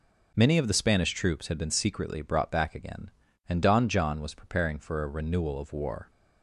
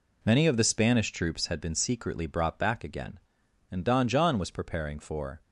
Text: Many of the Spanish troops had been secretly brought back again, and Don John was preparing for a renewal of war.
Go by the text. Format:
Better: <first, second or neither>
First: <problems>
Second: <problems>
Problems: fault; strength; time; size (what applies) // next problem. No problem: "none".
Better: first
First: none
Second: stops before "a renewal of war"; at 5.4 s